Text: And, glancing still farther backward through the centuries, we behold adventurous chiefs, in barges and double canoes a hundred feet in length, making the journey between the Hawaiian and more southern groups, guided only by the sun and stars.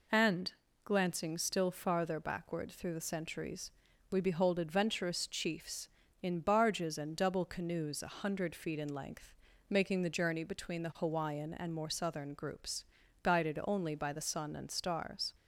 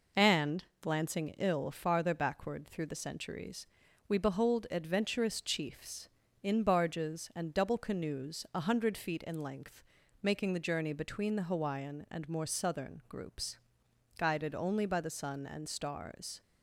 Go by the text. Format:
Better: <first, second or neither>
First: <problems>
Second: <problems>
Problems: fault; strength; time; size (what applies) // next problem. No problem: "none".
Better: first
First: none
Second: says "ill" for "still"; at 1.3 s